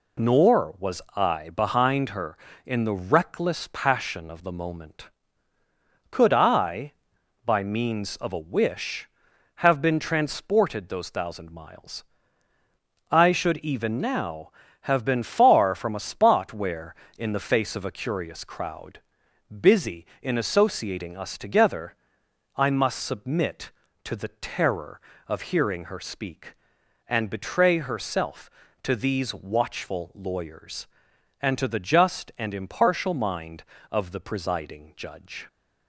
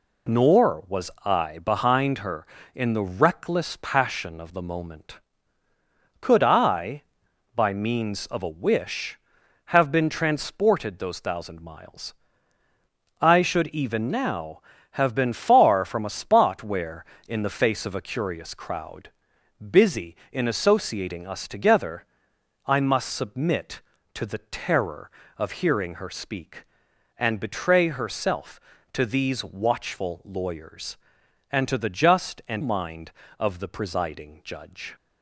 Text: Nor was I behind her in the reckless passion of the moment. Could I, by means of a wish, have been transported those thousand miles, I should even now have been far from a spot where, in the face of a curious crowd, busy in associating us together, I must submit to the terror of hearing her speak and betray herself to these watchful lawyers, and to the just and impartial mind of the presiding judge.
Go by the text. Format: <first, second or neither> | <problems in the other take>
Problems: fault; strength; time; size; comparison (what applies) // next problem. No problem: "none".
first | skips "impartial"; at 32.6 s